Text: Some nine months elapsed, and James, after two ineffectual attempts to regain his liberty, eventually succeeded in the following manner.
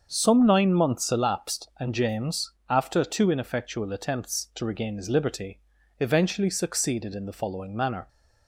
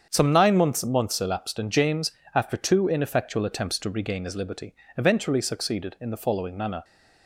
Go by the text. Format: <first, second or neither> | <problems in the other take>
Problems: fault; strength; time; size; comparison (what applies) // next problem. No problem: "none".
first | starts louder than the rest; strong; until 1.1 s; 7.5 dB; also in the first // says "months" twice; at 0.8 s